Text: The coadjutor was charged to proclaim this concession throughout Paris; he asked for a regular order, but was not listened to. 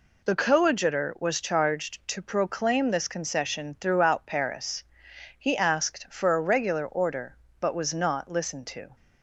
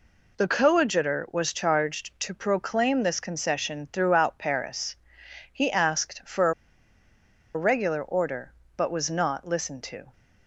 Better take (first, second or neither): first